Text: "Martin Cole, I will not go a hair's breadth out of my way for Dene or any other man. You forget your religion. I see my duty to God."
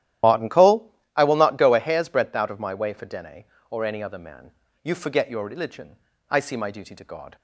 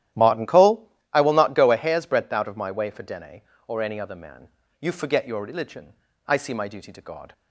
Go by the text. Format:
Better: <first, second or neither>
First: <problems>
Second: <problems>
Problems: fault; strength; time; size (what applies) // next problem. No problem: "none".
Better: second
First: loses the start of "Martin"; at 0.2 s; 60 ms // starts louder than the rest; strong; until 1.4 s; 12.5 dB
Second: starts louder than the rest; strong; until 1.3 s; 12 dB